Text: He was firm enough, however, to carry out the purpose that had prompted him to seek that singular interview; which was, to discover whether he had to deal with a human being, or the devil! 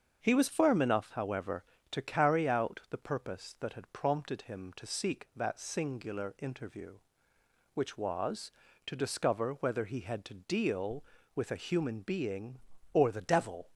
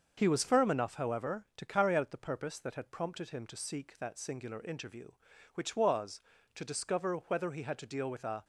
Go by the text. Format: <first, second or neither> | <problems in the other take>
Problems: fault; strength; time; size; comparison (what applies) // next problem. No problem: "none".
first | starts louder than the rest; until 1.1 s; 6.5 dB; also in the first // stops before "human being or the devil"; at 8.4 s